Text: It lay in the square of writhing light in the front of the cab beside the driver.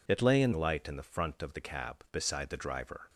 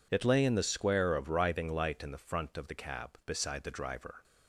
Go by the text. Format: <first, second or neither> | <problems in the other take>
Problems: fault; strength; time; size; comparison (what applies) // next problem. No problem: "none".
second | skips "the square of writhing"; at 0.5 s